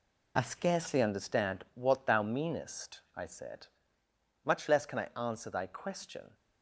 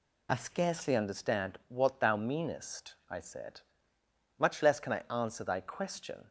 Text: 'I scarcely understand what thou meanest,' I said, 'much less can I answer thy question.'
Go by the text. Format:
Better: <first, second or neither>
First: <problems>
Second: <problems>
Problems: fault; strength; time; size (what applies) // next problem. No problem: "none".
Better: second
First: gets quieter; throughout; 7 dB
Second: none